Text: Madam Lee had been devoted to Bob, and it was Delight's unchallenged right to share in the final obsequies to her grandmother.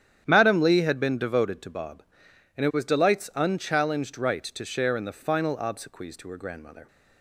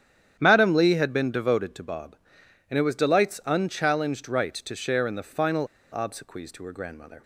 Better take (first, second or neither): first